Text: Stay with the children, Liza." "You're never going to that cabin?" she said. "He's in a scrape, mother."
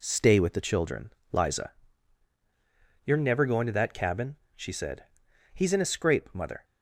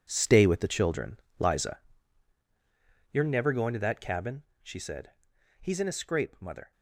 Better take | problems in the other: first | gets quieter; strong; throughout; 13.5 dB

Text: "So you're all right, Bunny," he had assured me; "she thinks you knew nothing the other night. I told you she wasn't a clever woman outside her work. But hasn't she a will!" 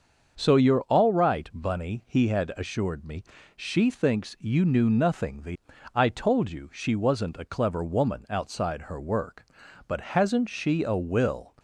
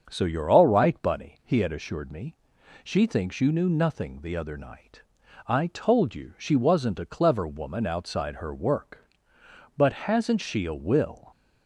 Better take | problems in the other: second | starts louder than the rest; until 1.3 s; 6.5 dB; also in the second // skips "other night"; at 5.7 s

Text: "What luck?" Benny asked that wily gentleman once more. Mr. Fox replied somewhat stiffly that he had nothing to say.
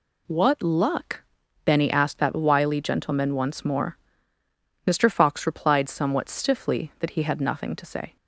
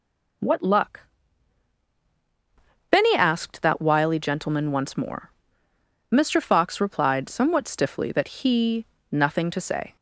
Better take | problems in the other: first | skips "had"; at 8.9 s

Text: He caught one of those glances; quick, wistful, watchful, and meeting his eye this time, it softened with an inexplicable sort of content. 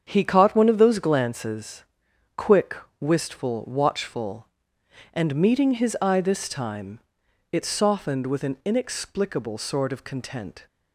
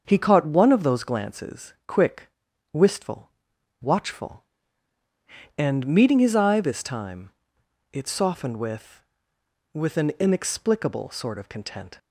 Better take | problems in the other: first | starts louder than the rest; until 1.0 s; 6.5 dB; strong in the first // says "with" twice; at 9.7 s

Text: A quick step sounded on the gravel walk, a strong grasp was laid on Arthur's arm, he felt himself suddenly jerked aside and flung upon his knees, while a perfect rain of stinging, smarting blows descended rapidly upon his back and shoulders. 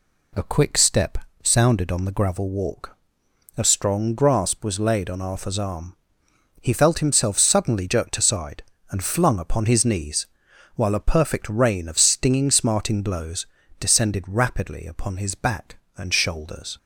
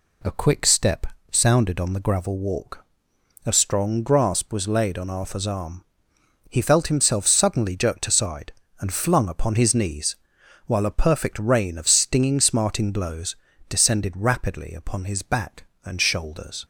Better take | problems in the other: neither | pauses between "step" and "sounded"; slight; the same in both // pauses between "blows" and "descended"; slight; the same in both

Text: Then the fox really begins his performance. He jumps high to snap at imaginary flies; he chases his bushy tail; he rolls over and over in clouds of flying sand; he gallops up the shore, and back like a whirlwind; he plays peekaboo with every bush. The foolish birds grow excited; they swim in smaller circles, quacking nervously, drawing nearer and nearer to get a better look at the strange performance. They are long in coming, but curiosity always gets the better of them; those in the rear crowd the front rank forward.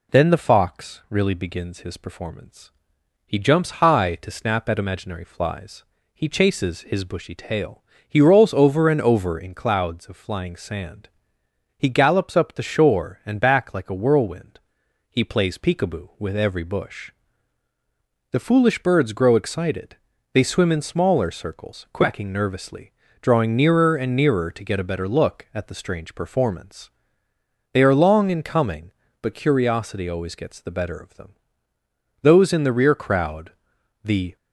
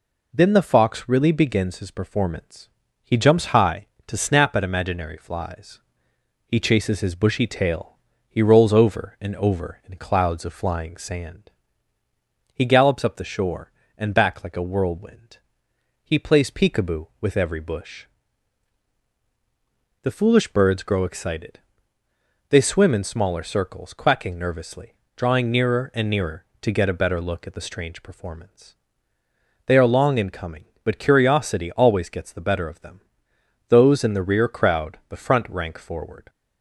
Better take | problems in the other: second | pauses between "crowd" and "the"; noticeable; at 33.5 s; 0.52 s long // stops before "front rank forward"; at 34.3 s

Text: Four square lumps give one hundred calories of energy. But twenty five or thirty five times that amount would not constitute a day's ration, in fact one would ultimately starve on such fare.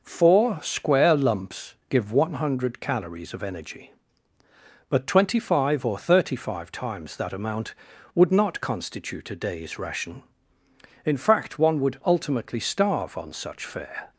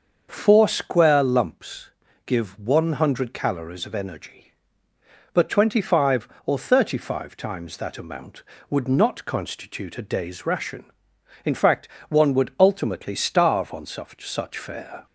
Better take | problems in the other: first | starts louder than the rest; until 1.3 s; 6.5 dB // pauses between "lumps" and "give"; slight; at 1.8 s; 0.36 s long // pauses between "fact" and "one"; slight; at 11.8 s; 0.22 s long // says "such" twice; at 14.2 s

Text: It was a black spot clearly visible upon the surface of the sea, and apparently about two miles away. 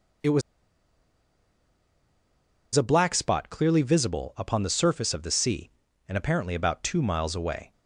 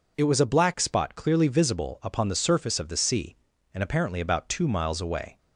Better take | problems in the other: second | pauses between "was" and "a"; strong; at 0.4 s; 2.3 s long

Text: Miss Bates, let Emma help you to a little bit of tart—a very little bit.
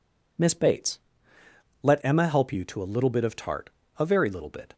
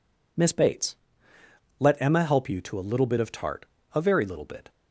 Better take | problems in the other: neither | none

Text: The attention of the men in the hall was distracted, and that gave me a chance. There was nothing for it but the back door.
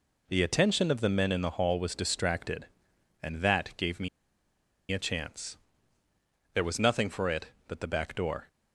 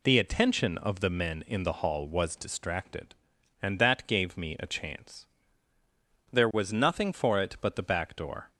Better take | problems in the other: second | pauses between "me" and "a"; noticeable; at 4.0 s; 0.82 s long

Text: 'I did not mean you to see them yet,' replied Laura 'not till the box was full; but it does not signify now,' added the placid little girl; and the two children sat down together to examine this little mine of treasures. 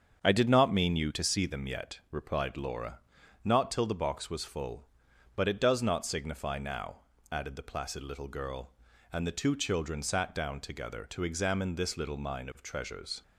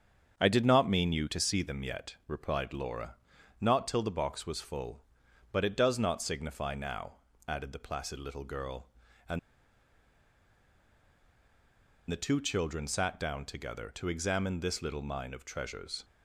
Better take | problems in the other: first | starts louder than the rest; strong; until 1.4 s; 7.5 dB; strong in the first // pauses between "Laura" and "not"; at 3.1 s; 0.42 s long; also in the first // pauses between "and" and "the"; strong; at 9.3 s; 2.7 s long

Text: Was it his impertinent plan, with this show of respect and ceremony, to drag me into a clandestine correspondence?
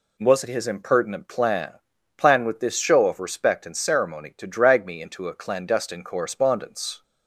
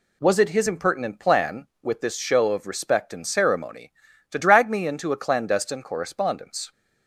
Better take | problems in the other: second | says "plan" twice; at 2.1 s

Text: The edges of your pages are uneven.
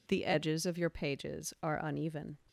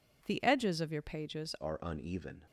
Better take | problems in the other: first | changes voice at "are"; from 1.6 s on; 0.8 s long

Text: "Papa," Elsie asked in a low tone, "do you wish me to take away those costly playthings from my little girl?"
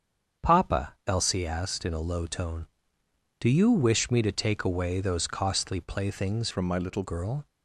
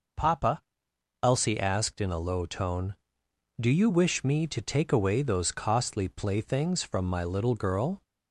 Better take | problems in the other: second | starts louder than the rest; strong; until 1.5 s; 7.5 dB // changes voice from "from" to "little"; from 6.5 to 7.0 s; 0.5 s long

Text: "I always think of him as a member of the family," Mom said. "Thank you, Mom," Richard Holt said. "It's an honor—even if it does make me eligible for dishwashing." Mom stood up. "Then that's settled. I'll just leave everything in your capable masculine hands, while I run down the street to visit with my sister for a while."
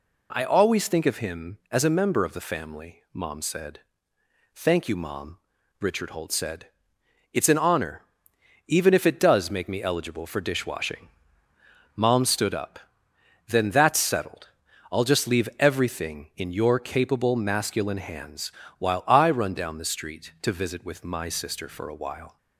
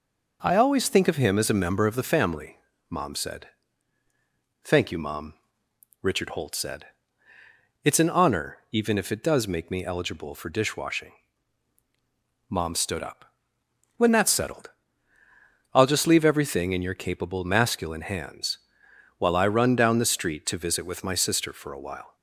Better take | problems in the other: first | says "When" for "Then"; at 13.9 s

